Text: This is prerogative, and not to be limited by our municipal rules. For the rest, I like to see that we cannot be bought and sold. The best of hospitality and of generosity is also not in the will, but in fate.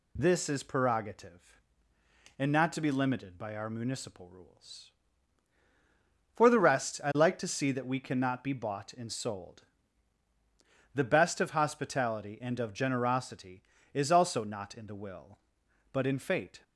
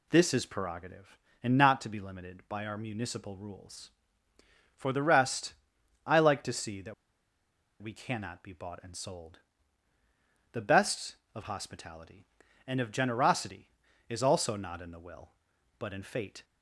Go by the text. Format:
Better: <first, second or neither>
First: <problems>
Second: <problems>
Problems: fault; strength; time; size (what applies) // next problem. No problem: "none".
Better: first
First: none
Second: pauses between "that" and "we"; noticeable; at 6.9 s; 0.87 s long